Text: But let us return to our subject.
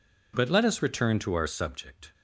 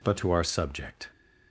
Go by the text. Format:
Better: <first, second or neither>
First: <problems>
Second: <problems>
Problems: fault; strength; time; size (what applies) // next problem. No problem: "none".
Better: first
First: none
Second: skips "let us return"; at 0.1 s